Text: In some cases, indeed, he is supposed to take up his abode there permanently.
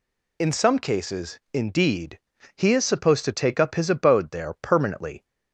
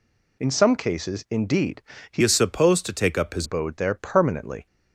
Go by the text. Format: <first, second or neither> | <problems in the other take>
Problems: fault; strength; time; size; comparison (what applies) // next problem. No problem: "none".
first | changes voice from "is" to "his"; from 2.2 to 3.4 s; 1.2 s long